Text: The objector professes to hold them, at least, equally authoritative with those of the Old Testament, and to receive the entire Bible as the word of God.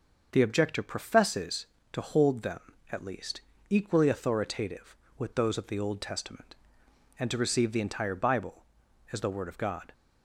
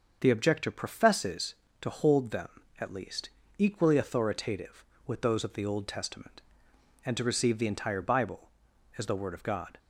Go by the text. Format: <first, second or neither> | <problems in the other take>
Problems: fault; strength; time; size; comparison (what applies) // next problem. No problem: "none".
neither | starts louder than the rest; the same in both